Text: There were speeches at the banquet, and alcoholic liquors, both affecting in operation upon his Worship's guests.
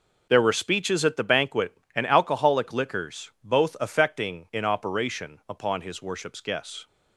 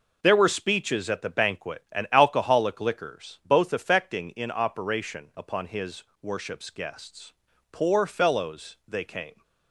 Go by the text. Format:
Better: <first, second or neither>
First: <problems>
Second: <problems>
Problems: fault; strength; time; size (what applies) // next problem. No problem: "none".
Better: first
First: none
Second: pauses between "his" and "Worship's"; slight; at 6.0 s; 0.22 s long // goes on to say "Poor fellows they came"; strong; from 7.7 s on; 1.7 s long